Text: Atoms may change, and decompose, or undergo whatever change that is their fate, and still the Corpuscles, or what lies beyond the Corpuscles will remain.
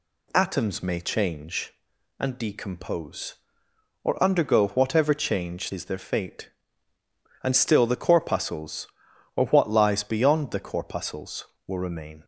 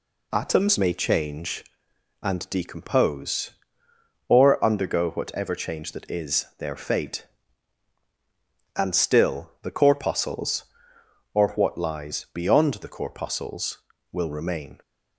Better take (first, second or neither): second